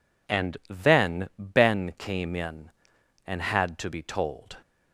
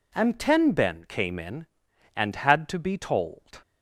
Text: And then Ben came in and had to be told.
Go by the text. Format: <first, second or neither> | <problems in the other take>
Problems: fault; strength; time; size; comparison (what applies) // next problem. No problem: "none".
first | says "ten" for "then"; at 0.3 s